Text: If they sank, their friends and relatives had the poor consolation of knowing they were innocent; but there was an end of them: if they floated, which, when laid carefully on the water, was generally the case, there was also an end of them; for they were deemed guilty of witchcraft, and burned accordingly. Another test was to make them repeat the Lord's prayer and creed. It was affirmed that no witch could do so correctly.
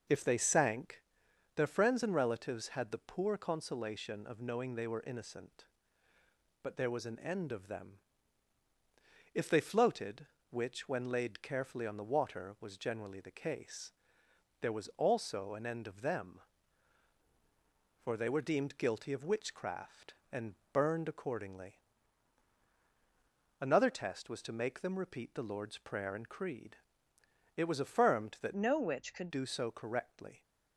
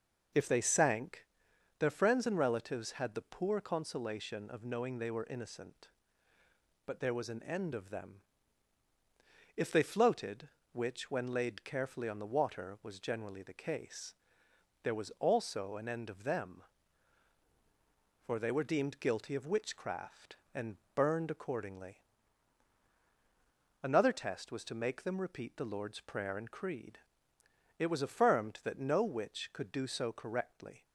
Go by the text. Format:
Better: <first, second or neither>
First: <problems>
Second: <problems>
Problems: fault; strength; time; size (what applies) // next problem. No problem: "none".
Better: second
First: starts louder than the rest; noticeable; until 1.6 s; 6 dB // pauses between "and" and "burned"; slight; at 20.5 s; 0.16 s long // changes voice from "no" to "could"; from 28.5 to 29.2 s; 0.7 s long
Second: starts louder than the rest; noticeable; until 1.8 s; 6 dB // pauses between "and" and "burned"; slight; at 20.7 s; 0.16 s long